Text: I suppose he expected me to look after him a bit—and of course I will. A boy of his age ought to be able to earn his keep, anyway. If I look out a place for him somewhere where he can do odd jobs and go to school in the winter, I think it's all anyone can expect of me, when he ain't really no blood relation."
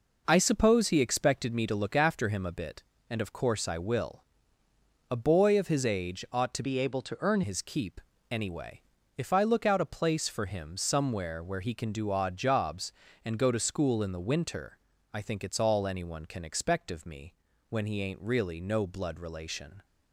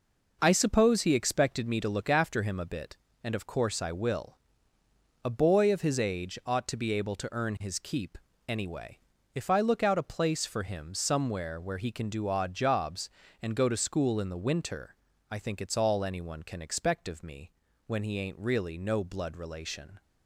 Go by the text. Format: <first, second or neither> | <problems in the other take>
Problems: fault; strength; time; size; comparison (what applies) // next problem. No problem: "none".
second | changes voice from "be" to "earn"; from 6.6 to 7.4 s; 0.8 s long